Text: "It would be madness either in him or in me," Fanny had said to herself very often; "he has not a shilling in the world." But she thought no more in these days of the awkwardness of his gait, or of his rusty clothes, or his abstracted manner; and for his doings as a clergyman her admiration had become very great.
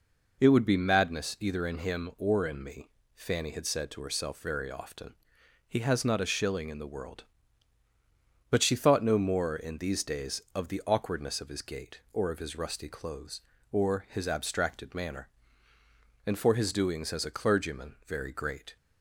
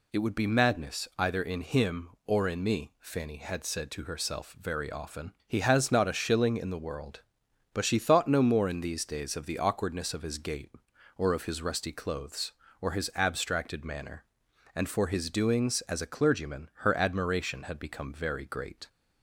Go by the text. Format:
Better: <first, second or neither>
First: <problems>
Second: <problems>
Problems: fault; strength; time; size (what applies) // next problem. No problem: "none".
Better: second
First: skips "her admiration had become"; at 18.0 s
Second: none